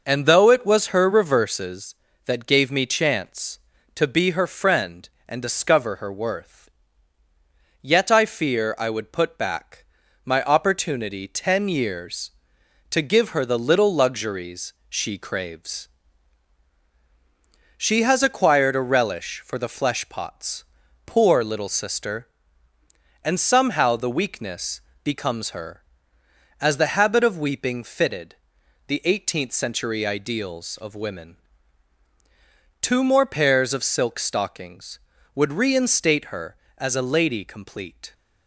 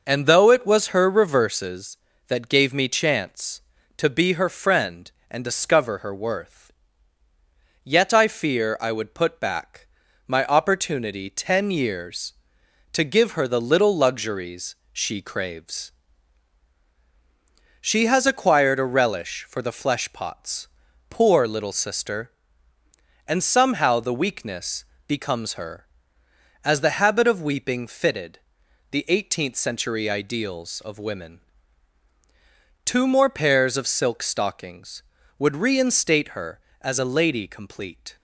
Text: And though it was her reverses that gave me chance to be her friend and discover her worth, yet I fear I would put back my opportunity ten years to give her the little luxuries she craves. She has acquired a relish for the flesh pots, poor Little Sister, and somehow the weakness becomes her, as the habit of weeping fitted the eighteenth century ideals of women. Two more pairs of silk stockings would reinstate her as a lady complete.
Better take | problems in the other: neither | pauses between "back" and "my"; the same in both // pauses between "luxuries" and "she"; slight; the same in both // pauses between "weakness" and "becomes"; slight; the same in both // pauses between "fitted" and "the"; noticeable; the same in both

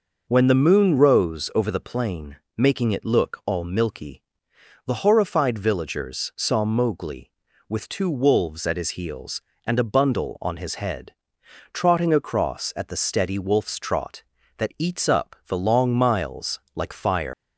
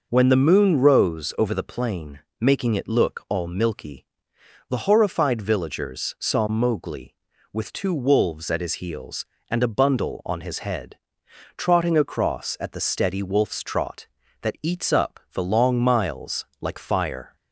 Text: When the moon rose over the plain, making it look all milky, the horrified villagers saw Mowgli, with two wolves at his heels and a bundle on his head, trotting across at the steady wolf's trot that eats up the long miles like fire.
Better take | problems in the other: second | pauses between "miles" and "like"; slight; at 16.5 s; 0.16 s long; slight in the second // leaves "fire" unfinished; at 17.3 s; 165 ms

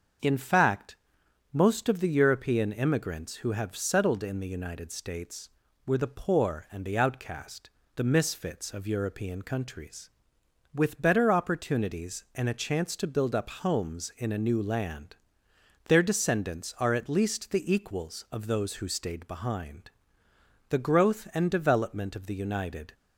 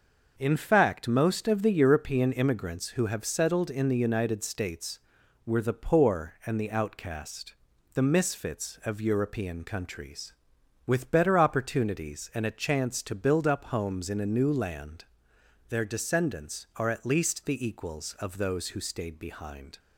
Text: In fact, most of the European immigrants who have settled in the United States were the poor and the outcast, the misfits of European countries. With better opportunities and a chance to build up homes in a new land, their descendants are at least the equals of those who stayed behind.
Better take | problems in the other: second | starts louder than the rest; until 1.7 s; 7 dB; noticeable in the second // goes on to say "The growth and development of the United"; strong; from 20.6 s on; 2.2 s long

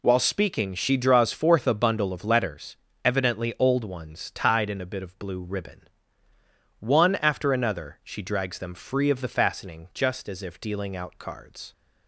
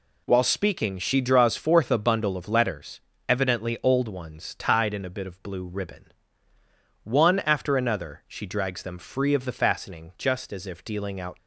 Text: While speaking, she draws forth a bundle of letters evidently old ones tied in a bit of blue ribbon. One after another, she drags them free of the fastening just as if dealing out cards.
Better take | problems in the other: first | pauses between "letters" and "evidently"; slight; at 3.0 s; 0.26 s long; slight in the first // stops before "cards"; at 11.3 s

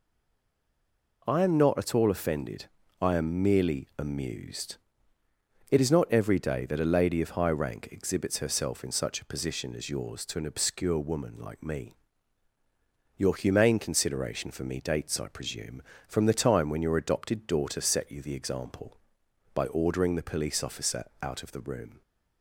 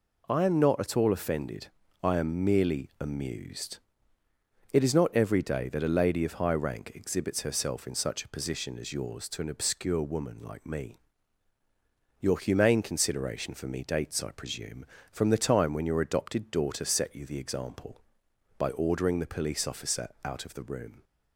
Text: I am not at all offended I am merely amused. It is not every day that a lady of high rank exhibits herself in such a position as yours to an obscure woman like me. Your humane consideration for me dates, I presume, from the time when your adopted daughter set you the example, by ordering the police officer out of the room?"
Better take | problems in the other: second | stays silent before the first word; noticeable; until 1.2 s; 1.2 s long // pauses between "offended" and "I"; slight; at 2.6 s; 0.34 s long; slight in the second // pauses between "officer" and "out"; slight; at 21.0 s; 0.16 s long

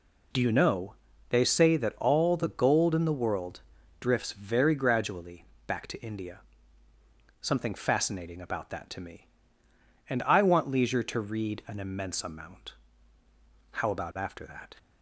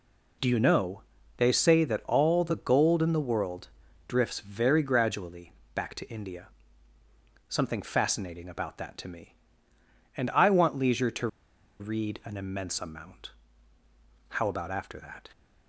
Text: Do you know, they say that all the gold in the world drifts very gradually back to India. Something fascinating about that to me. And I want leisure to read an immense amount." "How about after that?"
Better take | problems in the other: first | pauses between "world" and "drifts"; at 3.6 s; 0.40 s long; also in the first // pauses between "gradually" and "back"; slight; at 5.5 s; 0.22 s long; slight in the first // pauses between "to" and "read"; noticeable; at 11.2 s; 0.52 s long

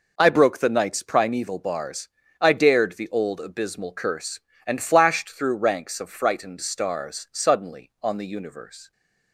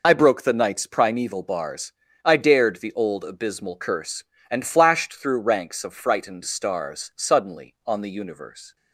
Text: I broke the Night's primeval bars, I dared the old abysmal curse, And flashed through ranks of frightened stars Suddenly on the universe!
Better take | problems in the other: first | loses the start of "I"; at 0.0 s; 35 ms

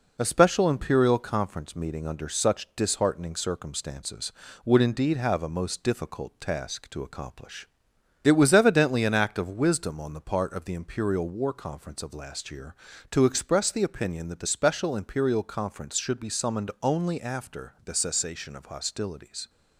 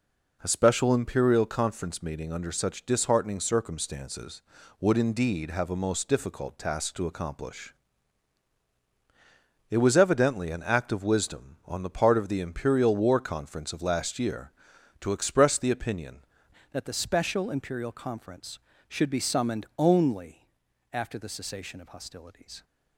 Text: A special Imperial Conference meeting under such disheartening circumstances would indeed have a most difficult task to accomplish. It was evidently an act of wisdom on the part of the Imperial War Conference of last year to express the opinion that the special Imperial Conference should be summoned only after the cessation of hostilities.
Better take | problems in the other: first | changes voice at "that"; from 16.7 s on; 5.9 s long // pauses between "only" and "after"; at 20.4 s; 0.44 s long

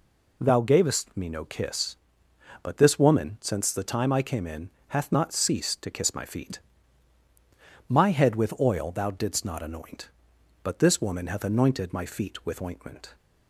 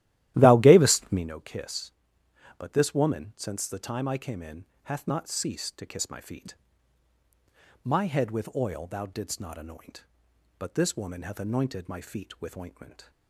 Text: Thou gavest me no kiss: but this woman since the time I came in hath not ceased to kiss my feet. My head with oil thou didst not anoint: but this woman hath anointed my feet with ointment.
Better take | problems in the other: first | starts louder than the rest; strong; until 1.3 s; 14 dB // pauses between "in" and "hath"; slight; at 4.6 s; 0.20 s long; slight in the first

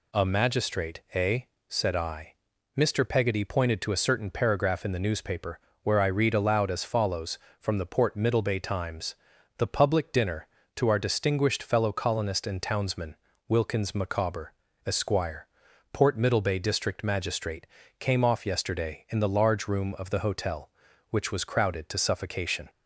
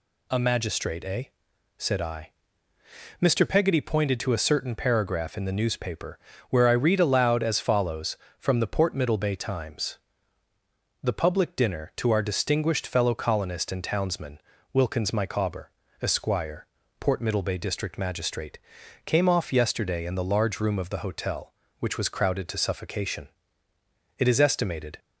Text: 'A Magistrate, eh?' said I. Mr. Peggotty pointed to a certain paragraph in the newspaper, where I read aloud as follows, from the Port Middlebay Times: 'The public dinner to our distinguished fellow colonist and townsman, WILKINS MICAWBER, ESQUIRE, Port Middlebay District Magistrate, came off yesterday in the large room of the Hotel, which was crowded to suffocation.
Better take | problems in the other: first | goes on to say "It is estimated"; noticeable; from 24.1 s on; 0.80 s long

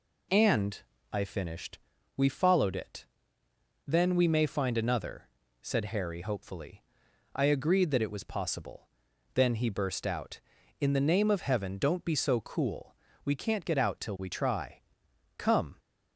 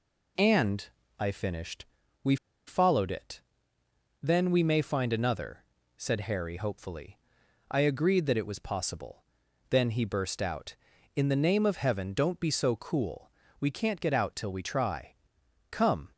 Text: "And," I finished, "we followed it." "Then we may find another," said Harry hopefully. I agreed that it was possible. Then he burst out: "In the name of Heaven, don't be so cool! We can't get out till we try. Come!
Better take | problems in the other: first | pauses between "we" and "followed"; slight; at 2.3 s; 0.31 s long

